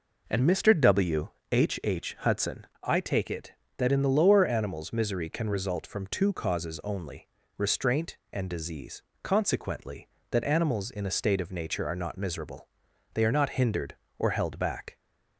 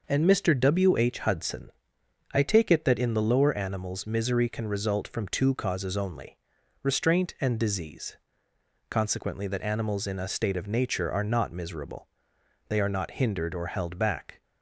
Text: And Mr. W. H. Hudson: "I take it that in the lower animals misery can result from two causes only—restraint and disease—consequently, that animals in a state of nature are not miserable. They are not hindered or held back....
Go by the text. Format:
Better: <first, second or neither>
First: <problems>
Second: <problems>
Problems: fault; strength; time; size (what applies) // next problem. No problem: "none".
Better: second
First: says "H" twice; at 1.8 s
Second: none